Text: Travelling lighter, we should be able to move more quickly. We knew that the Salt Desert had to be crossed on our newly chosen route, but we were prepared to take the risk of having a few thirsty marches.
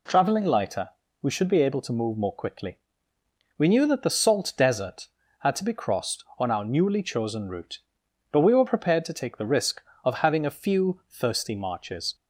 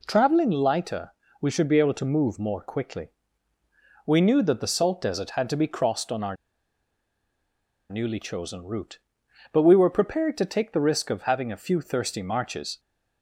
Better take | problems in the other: first | pauses between "our" and "newly"; strong; at 6.3 s; 1.5 s long

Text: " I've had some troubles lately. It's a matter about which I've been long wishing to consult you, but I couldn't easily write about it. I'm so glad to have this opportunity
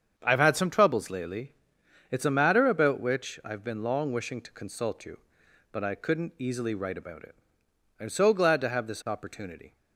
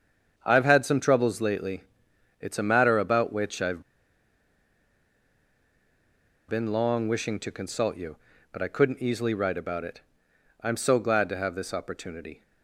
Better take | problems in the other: first | starts louder than the rest; strong; until 1.3 s; 7.5 dB; strong in the first // pauses between "I've" and "been"; strong; at 3.8 s; 2.6 s long

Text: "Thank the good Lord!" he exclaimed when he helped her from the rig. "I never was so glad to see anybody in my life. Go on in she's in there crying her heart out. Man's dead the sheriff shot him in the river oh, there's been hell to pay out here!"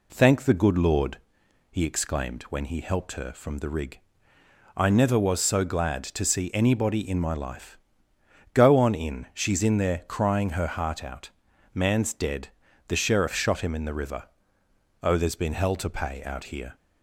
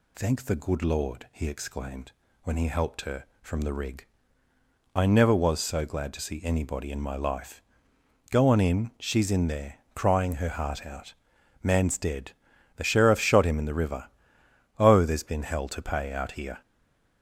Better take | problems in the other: first | pauses between "exclaimed" and "when"; slight; at 2.1 s; 0.30 s long // pauses between "dead" and "the"; noticeable; at 12.3 s; 0.46 s long; also in the first // pauses between "river" and "oh"; noticeable; at 14.0 s; 0.70 s long; noticeable in the first // stays silent after the last word; slight; from 16.6 s on; 0.6 s long

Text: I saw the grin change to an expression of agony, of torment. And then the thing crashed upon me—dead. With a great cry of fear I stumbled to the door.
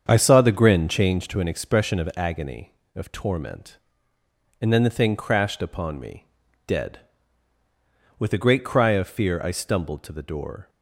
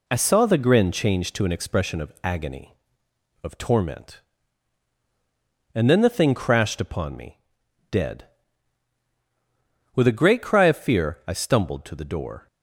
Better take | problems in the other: second | starts louder than the rest; strong; until 1.2 s; 7.5 dB

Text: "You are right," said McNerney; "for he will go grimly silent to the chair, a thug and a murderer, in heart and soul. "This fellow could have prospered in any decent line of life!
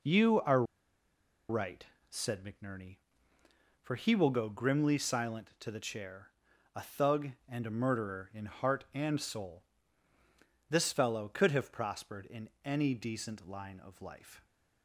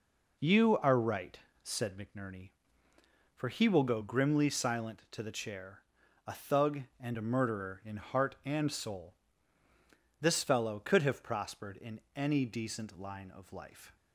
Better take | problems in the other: second | pauses between "are" and "right"; noticeable; at 0.6 s; 0.86 s long // pauses between "in" and "any"; slight; at 12.5 s; 0.16 s long; slight in the second

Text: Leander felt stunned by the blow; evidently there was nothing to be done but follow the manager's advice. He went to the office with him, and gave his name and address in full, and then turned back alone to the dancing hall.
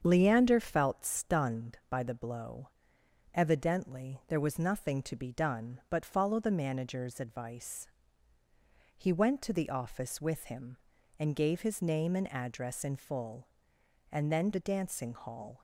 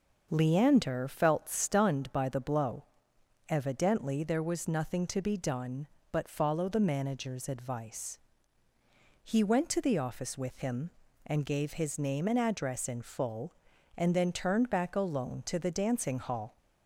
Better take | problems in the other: second | starts louder than the rest; strong; until 1.0 s; 7.5 dB; noticeable in the second // skips "turned back alone to"; at 14.5 s

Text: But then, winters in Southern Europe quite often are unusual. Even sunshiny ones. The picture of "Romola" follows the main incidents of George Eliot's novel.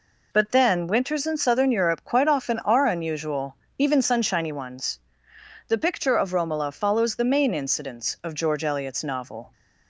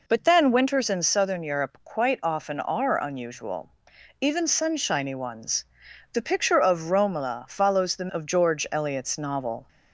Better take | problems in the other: first | skips "main incidents"; at 8.0 s

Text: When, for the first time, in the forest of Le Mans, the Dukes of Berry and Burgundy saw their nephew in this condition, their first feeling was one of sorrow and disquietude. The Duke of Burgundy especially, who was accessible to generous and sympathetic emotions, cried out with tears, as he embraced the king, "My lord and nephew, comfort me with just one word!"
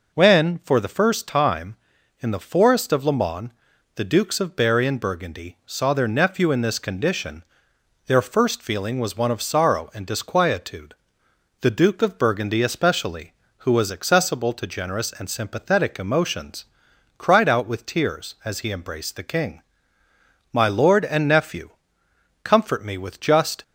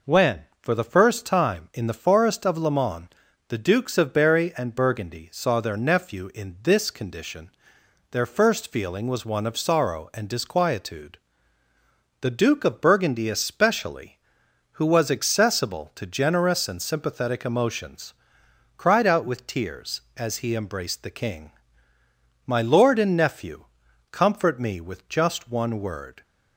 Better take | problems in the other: second | stops before "one word"; at 23.6 s

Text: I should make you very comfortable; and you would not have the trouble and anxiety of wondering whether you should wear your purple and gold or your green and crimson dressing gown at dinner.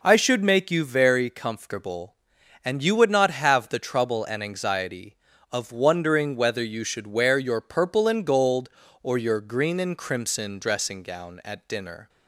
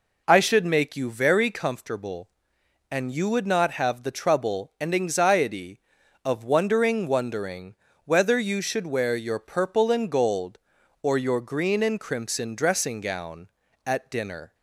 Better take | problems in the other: first | says "wondering" twice; at 7.0 s

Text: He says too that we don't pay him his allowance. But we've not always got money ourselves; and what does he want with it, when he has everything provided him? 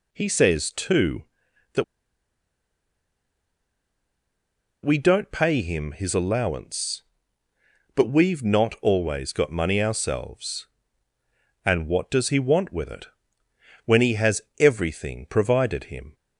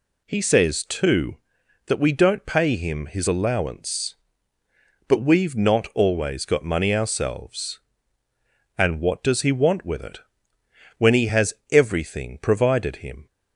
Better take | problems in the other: second | pauses between "that" and "we"; strong; at 1.8 s; 2.9 s long // pauses between "has" and "everything"; slight; at 14.4 s; 0.18 s long; slight in the second

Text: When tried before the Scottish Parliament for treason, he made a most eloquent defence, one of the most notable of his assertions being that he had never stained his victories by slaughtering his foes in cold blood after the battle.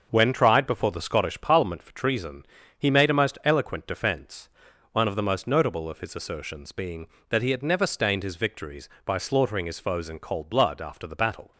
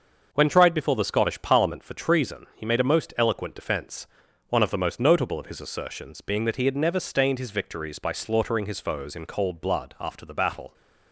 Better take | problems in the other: neither | starts louder than the rest; the same in both

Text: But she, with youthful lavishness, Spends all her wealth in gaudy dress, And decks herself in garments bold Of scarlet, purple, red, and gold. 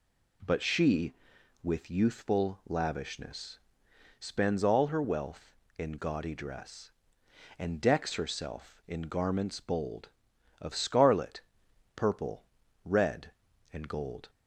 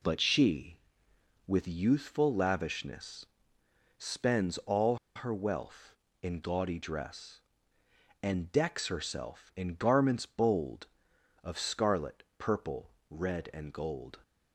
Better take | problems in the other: first | pauses between "all" and "her"; slight; at 4.9 s; 0.18 s long

